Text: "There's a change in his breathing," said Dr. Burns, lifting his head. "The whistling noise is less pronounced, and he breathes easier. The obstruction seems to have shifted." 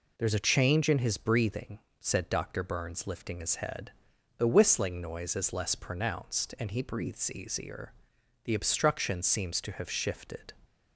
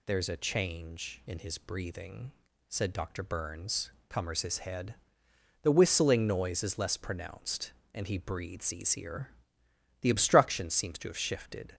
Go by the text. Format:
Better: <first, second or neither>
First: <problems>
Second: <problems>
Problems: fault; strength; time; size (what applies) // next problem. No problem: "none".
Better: first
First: none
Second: says "cummers" for "lifting"; at 4.0 s